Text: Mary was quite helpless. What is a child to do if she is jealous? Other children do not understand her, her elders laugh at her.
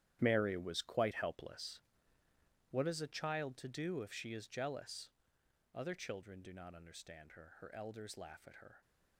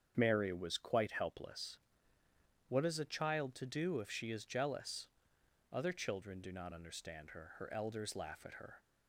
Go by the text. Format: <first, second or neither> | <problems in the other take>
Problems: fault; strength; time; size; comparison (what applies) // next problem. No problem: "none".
second | gets quieter; strong; throughout; 12.5 dB // starts louder than the rest; strong; until 1.2 s; 11.5 dB; strong in the second